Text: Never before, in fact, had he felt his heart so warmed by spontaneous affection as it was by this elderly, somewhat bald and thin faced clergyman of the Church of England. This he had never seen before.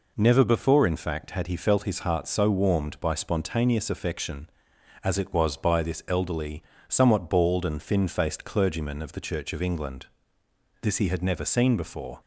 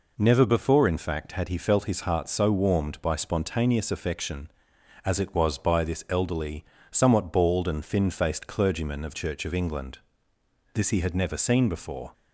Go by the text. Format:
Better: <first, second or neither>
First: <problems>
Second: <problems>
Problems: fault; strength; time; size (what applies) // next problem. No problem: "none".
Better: first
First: none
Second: skips "the"; at 9.1 s